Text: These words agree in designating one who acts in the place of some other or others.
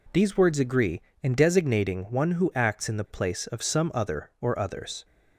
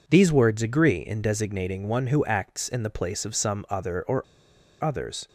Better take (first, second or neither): first